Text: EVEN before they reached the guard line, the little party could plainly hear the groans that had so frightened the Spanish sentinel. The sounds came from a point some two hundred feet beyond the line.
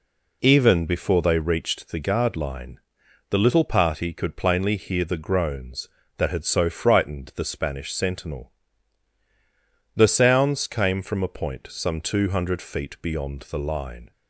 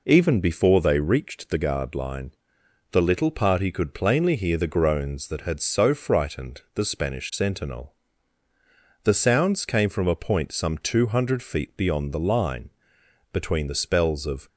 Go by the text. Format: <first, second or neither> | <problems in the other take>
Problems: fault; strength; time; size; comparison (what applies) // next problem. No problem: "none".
first | goes on to say "Between the spells of"; noticeable; from 13.3 s on; 1.1 s long